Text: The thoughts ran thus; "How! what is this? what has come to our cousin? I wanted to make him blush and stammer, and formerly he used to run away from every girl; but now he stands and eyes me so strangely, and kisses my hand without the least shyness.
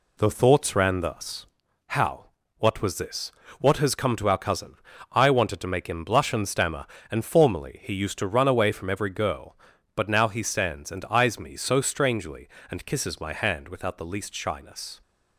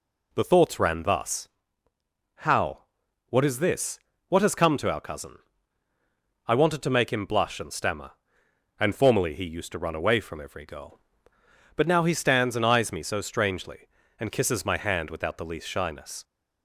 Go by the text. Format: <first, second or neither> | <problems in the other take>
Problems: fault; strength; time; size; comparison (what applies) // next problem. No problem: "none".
second | says "was" for "is"; at 2.8 s